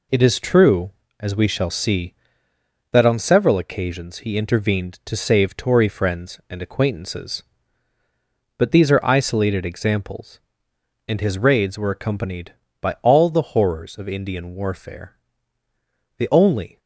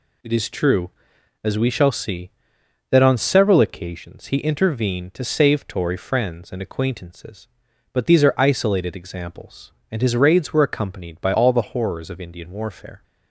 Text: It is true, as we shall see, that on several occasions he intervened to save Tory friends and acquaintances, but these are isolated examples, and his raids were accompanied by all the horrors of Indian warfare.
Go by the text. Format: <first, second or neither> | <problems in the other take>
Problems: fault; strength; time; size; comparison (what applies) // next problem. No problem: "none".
second | goes on to say "The only"; noticeable; from 16.1 s on; 0.62 s long